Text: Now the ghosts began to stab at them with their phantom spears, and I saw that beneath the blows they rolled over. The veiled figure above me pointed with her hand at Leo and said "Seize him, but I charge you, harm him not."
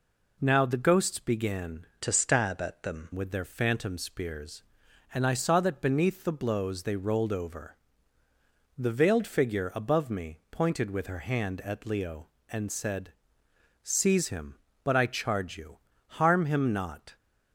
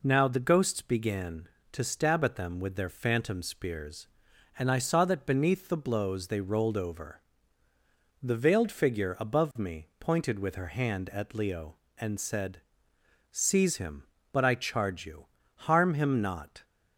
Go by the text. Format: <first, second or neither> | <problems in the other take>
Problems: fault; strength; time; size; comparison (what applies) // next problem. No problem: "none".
second | changes voice from "to" to "them"; from 2.0 to 3.0 s; 1.0 s long // pauses between "said" and "Seize"; noticeable; at 13.1 s; 0.72 s long; noticeable in the second